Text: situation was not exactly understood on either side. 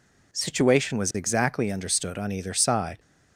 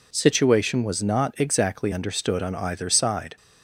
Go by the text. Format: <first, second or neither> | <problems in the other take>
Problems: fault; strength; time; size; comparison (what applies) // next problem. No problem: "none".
second | skips "not"; at 1.1 s